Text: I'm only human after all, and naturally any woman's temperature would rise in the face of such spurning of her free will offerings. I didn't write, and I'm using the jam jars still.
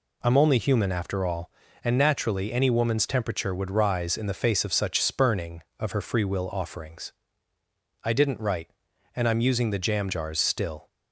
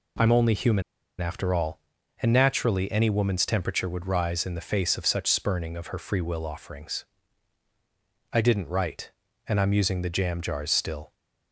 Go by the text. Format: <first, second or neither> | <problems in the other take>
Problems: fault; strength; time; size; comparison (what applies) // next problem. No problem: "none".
first | pauses between "human" and "after"; at 0.8 s; 0.37 s long